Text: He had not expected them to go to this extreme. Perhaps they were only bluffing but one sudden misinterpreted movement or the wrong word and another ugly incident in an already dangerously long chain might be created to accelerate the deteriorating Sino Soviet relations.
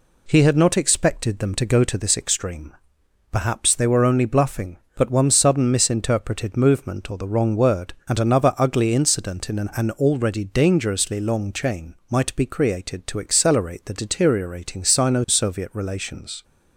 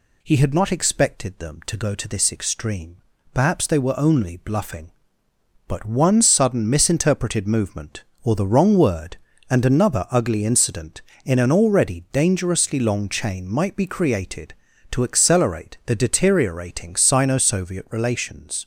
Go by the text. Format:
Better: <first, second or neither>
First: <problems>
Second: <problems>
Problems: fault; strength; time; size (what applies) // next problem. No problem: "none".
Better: second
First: says "an" twice; at 9.7 s // pauses between "chain" and "might"; slight; at 11.9 s; 0.16 s long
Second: none